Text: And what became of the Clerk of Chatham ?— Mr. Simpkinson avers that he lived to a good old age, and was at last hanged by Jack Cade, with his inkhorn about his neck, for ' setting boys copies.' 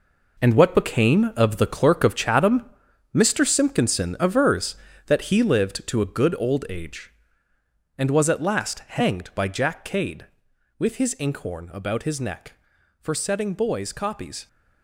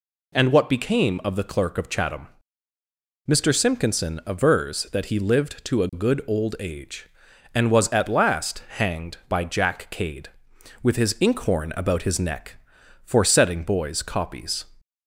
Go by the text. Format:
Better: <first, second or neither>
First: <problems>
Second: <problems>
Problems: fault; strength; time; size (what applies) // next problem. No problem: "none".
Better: second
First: gets quieter; strong; throughout; 10 dB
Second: none